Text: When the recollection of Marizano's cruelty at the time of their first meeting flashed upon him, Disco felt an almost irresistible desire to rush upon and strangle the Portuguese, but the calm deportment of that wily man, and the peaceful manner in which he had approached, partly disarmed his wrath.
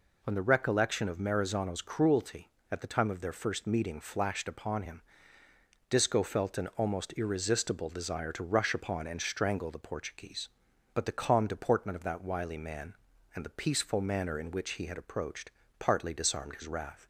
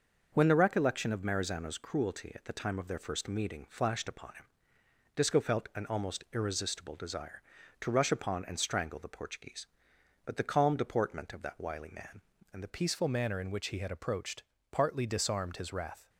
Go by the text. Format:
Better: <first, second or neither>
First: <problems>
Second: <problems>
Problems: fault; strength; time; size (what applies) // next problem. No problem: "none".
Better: first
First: none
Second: changes voice at "peaceful"; from 12.6 s on; 3.4 s long